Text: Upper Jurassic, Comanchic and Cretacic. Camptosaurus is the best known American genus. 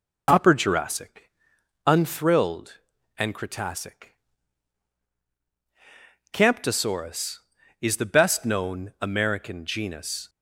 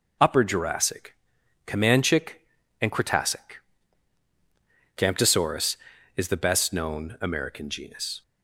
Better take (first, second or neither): second